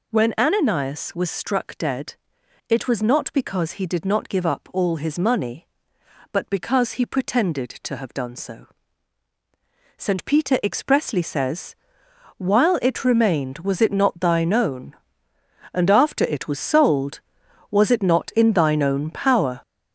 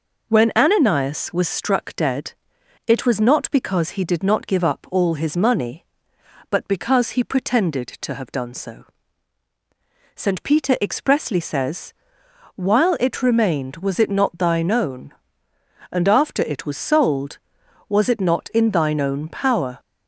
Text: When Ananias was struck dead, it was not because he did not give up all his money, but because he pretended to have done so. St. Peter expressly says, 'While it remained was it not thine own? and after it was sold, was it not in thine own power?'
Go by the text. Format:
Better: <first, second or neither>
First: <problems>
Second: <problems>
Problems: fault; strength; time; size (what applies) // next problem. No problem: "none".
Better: second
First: gets louder; noticeable; throughout; 6 dB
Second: none